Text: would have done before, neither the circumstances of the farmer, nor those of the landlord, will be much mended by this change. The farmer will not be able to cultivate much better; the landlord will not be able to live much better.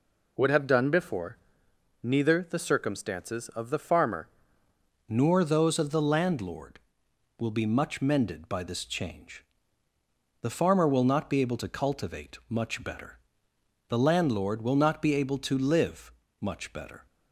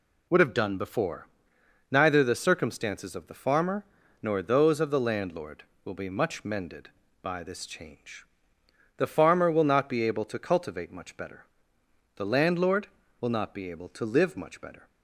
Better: second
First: changes voice at "nor"; from 5.0 s on; 12.0 s long // pauses between "live" and "much"; slight; at 16.0 s; 0.30 s long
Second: none

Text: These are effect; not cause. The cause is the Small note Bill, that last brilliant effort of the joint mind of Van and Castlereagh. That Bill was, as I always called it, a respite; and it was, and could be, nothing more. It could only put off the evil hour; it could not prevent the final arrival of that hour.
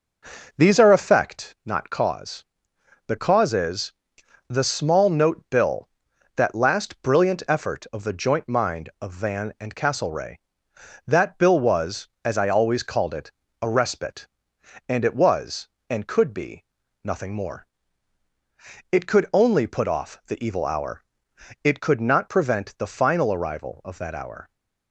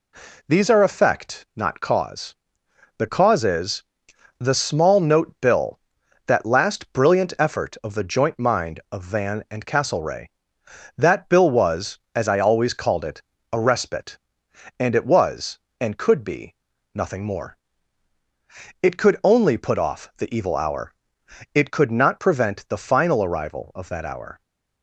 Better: second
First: starts louder than the rest; noticeable; until 1.2 s; 5 dB // pauses between "is" and "the"; noticeable; at 3.9 s; 0.56 s long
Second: pauses between "is" and "the"; noticeable; at 3.8 s; 0.56 s long

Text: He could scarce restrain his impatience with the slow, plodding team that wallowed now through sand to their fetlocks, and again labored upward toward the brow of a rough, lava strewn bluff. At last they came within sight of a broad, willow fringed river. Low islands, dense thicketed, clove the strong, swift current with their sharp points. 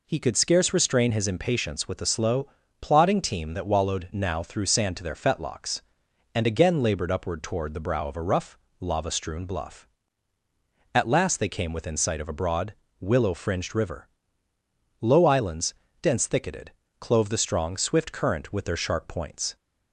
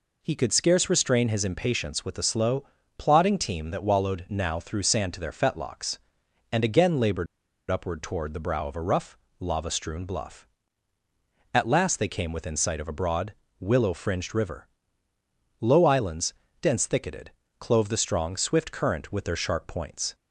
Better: first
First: none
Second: pauses between "labored" and "upward"; at 7.2 s; 0.44 s long

